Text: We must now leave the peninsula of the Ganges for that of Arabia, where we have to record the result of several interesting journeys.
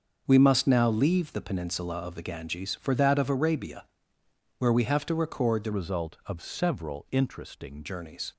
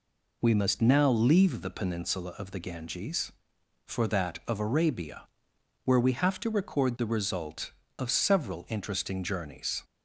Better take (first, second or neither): second